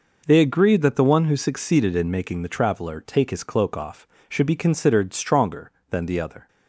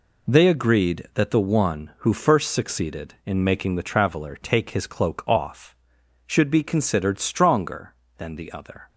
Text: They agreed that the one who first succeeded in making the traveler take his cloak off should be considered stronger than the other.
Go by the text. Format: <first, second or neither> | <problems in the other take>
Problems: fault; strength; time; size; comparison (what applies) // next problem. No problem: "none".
second | skips "first"; at 1.3 s